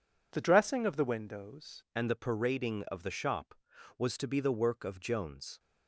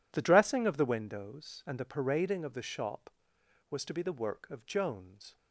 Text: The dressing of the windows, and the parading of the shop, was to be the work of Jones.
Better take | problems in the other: second | changes voice at "and"; from 1.9 s on; 3.6 s long

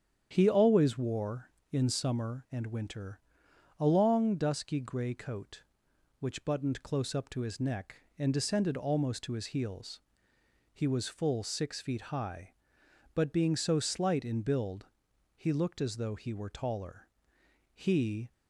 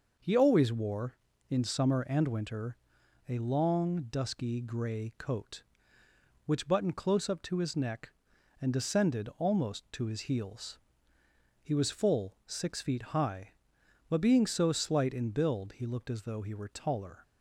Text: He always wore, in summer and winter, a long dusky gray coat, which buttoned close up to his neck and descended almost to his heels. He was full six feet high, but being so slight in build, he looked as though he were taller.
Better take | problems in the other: second | starts louder than the rest; strong; until 1.3 s; 8.5 dB // goes on to say "He"; from 17.7 s on; 0.58 s long

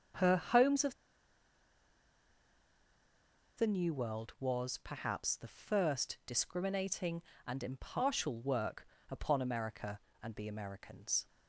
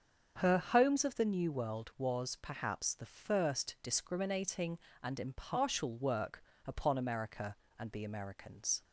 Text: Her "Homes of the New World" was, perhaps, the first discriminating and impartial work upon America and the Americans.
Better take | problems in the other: second | starts louder than the rest; until 3.7 s; 7 dB; also in the second // pauses between "of" and "the"; strong; at 0.9 s; 2.6 s long // pauses between "work" and "upon"; slight; at 8.8 s; 0.24 s long; slight in the second

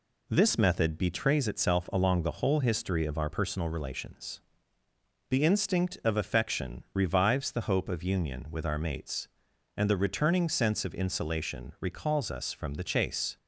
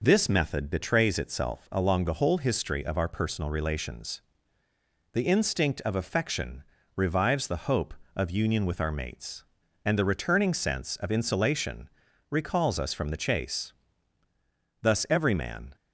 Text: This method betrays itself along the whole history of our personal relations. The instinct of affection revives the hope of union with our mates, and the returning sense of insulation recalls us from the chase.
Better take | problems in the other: first | pauses between "affection" and "revives"; slight; at 6.6 s; 0.32 s long // pauses between "insulation" and "recalls"; at 11.8 s; 0.44 s long // goes on to say "Thus every man"; noticeable; from 14.8 s on; 0.94 s long

